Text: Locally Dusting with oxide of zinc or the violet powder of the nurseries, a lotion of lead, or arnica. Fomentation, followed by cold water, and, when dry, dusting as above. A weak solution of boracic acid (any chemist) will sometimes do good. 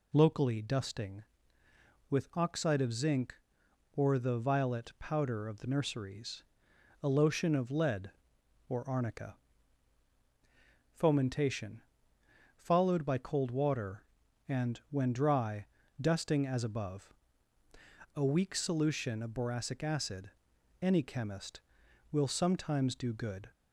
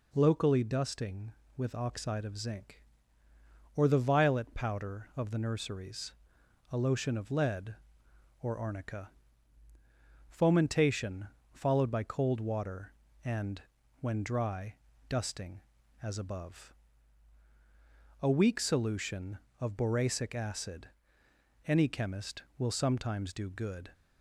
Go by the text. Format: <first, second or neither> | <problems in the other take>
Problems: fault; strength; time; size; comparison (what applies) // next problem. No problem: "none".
neither | none